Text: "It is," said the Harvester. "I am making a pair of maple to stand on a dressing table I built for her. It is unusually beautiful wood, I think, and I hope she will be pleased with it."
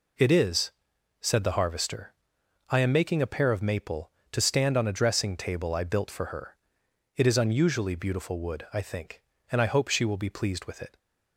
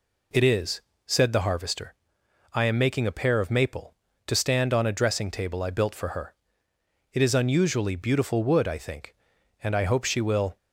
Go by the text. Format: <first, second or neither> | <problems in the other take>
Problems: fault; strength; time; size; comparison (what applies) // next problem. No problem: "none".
first | stops before "be pleased with it"; at 10.5 s